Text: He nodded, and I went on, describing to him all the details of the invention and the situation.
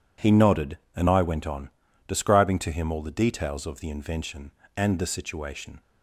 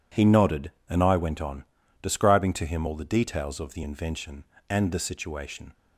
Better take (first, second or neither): neither